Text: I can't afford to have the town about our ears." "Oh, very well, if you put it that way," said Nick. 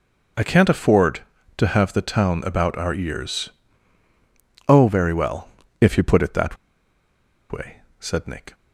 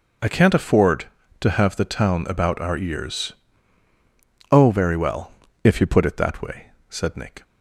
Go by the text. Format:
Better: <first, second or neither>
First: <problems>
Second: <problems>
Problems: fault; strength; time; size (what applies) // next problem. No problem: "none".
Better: second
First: pauses between "that" and "way"; noticeable; at 6.5 s; 0.95 s long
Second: none